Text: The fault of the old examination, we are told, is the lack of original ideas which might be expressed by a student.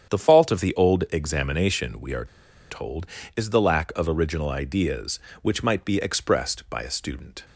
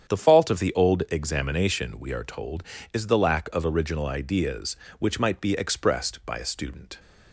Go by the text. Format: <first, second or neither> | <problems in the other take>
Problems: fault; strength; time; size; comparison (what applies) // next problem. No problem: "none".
second | starts louder than the rest; strong; until 1.1 s; 8.5 dB; strong in the second // pauses between "are" and "told"; at 2.2 s; 0.44 s long